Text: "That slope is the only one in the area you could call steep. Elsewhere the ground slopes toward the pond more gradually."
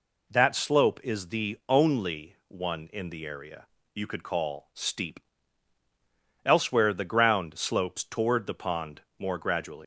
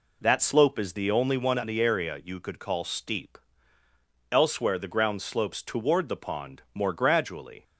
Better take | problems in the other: second | pauses between "area" and "you"; slight; at 3.6 s; 0.26 s long // pauses between "pond" and "more"; slight; at 9.0 s; 0.18 s long // leaves "gradually" unfinished; at 9.8 s; 145 ms

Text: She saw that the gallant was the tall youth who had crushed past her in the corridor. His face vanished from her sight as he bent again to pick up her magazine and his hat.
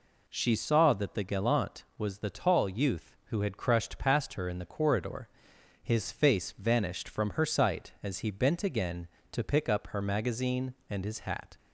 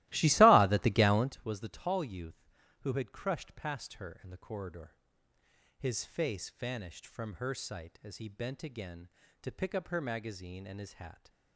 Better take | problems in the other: first | starts louder than the rest; strong; until 1.4 s; 17.5 dB

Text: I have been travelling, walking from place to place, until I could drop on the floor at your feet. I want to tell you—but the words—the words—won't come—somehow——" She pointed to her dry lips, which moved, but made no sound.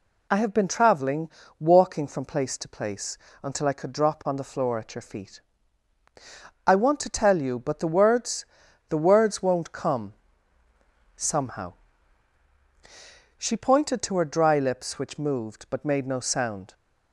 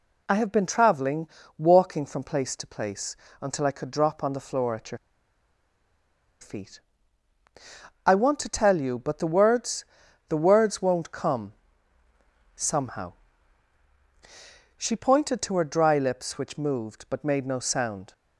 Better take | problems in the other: first | pauses between "your" and "feet"; strong; at 4.9 s; 1.4 s long

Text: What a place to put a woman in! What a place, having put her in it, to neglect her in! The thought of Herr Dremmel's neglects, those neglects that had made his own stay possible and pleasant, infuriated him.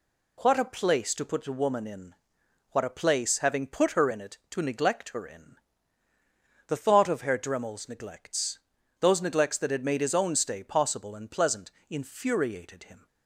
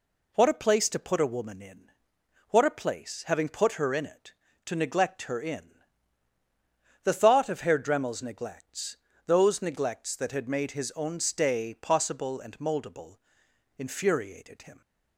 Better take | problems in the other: first | says "moldable" for "pleasant"; at 12.5 s

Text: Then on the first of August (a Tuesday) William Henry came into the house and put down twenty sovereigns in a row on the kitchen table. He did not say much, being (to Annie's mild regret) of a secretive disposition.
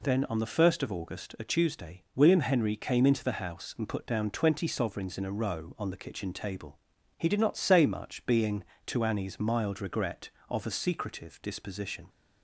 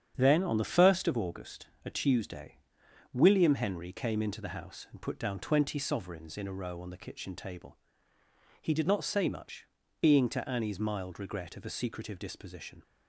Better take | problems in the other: first | gets quieter; throughout; 6.5 dB

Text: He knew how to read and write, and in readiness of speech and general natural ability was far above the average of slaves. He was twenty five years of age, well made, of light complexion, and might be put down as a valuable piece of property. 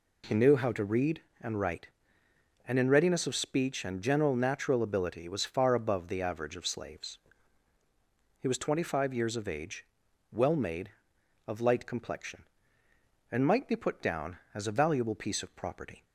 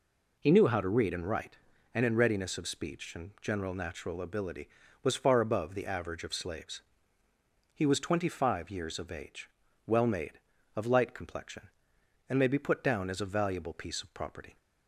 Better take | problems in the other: first | says "may" for "might"; at 12.3 s

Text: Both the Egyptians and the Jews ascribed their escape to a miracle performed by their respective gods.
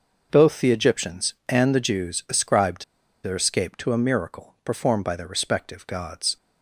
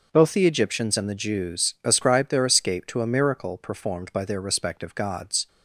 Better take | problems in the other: second | pauses between "ascribed" and "their"; at 2.8 s; 0.39 s long

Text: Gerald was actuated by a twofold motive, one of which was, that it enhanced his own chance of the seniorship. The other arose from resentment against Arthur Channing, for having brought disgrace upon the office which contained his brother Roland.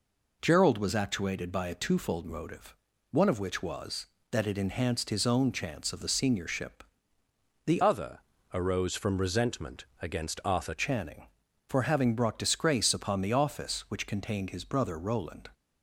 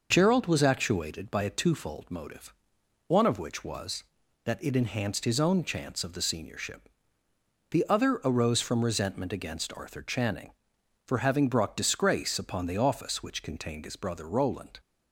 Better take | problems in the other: second | changes voice from "other" to "Arthur"; from 7.8 to 10.7 s; 2.9 s long // pauses between "other" and "arose"; slight; at 8.1 s; 0.34 s long // pauses between "resentment" and "against"; slight; at 9.8 s; 0.16 s long

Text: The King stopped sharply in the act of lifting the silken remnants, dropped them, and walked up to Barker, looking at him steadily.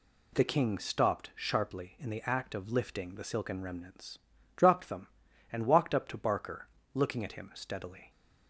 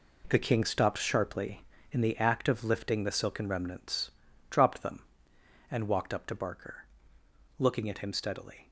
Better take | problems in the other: first | gets quieter; strong; throughout; 10 dB

